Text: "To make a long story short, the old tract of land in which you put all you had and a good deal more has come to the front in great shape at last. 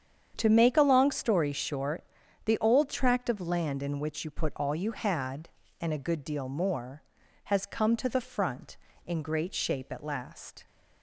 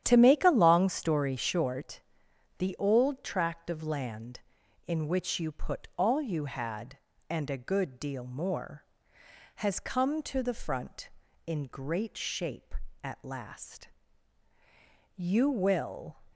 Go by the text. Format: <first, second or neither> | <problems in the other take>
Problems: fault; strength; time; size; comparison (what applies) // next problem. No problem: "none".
first | starts louder than the rest; strong; until 1.0 s; 10.5 dB; strong in the first // goes on to say "You will"; noticeable; from 15.1 s on; 1.0 s long